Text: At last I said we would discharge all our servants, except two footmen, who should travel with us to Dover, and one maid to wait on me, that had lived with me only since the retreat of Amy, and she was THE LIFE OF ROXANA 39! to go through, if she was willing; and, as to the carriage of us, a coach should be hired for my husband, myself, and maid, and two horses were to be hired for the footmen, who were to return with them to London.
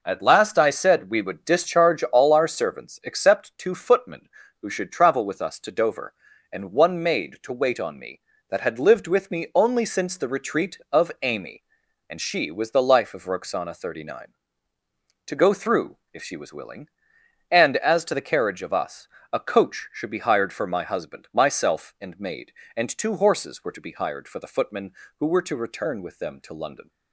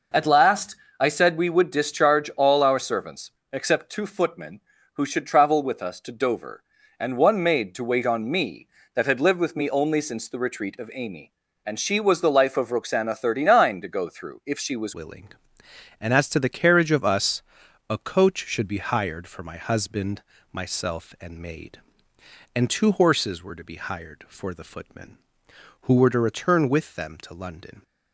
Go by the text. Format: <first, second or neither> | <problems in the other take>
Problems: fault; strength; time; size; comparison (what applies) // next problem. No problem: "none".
first | pauses between "last" and "I"; slight; at 0.7 s; 0.24 s long // changes voice at "willing"; from 14.9 s on; 12.9 s long